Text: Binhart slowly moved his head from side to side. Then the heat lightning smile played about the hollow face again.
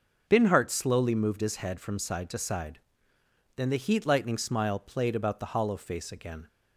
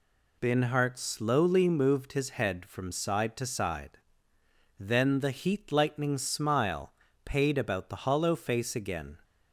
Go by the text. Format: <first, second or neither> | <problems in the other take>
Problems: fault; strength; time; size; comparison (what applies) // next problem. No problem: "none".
first | says "paid" for "played"; at 7.2 s